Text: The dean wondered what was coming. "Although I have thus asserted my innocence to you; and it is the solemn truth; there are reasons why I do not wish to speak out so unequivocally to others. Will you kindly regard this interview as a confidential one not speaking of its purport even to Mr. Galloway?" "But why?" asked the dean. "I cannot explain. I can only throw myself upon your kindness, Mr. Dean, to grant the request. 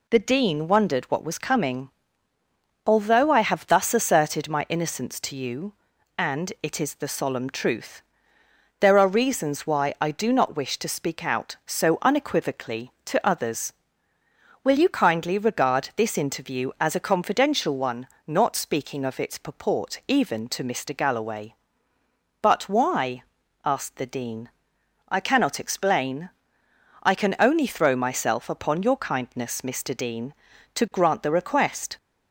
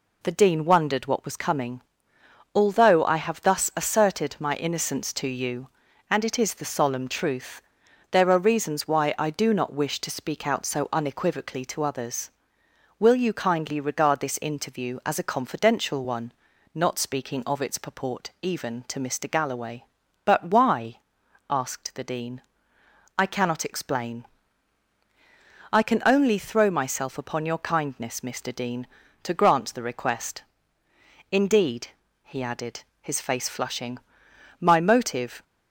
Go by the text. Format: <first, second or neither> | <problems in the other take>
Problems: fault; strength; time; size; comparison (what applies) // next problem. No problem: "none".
first | pauses between "one" and "not"; at 16.3 s; 0.40 s long; slight in the first // goes on to say "Indeed he added his face flushing my motive"; strong; from 31.3 s on; 4.1 s long